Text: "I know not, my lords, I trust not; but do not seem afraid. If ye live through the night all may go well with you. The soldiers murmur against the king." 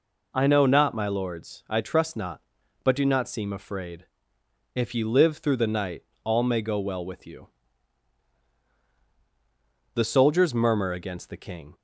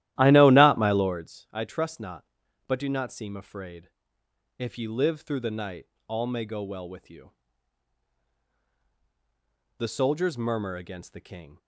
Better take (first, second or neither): first